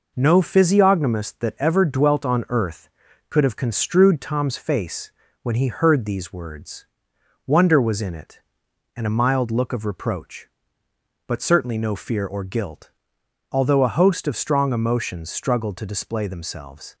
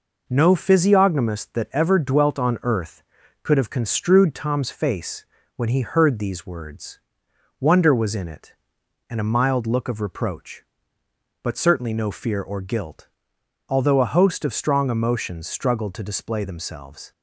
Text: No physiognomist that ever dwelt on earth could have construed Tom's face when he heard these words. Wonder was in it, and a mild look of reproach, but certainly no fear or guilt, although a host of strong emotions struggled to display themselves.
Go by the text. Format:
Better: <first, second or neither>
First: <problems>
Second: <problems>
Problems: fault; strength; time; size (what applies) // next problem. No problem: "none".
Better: neither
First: pauses between "face" and "when"; slight; at 5.1 s; 0.30 s long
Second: pauses between "face" and "when"; slight; at 5.2 s; 0.30 s long